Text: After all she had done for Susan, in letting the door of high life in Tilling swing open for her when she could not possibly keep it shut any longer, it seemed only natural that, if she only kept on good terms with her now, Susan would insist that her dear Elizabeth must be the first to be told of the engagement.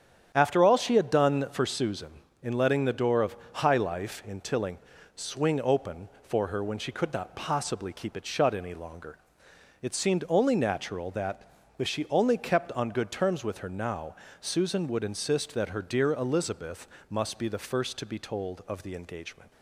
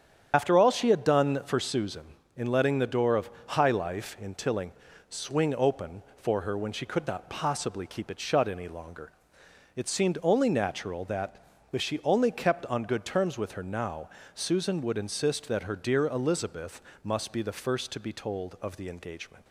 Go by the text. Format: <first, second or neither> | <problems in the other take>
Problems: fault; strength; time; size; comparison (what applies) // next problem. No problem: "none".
first | loses the start of "After"; at 0.3 s; 60 ms // starts louder than the rest; strong; until 1.3 s; 8.5 dB; strong in the first // pauses between "of" and "high"; slight; at 3.2 s; 0.20 s long; slight in the first // pauses between "Tilling" and "swing"; at 4.7 s; 0.38 s long; also in the first // pauses between "Elizabeth" and "must"; slight; at 16.8 s; 0.22 s long; slight in the first